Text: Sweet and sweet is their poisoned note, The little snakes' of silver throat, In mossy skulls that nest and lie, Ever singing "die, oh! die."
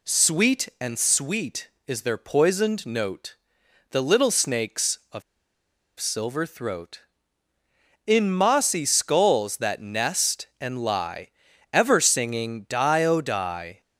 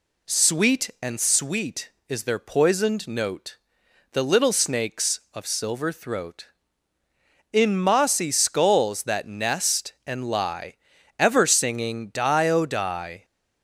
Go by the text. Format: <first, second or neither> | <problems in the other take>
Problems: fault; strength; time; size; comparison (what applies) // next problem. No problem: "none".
second | pauses between "of" and "silver"; noticeable; at 5.2 s; 0.77 s long